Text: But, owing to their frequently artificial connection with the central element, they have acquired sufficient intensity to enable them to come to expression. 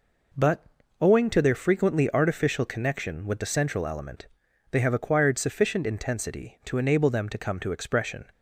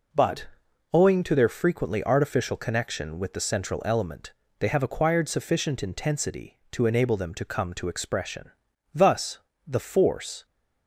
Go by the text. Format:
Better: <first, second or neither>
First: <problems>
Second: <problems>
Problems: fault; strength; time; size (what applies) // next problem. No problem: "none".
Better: first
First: none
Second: goes on to say "Thus the force"; from 8.9 s on; 1.5 s long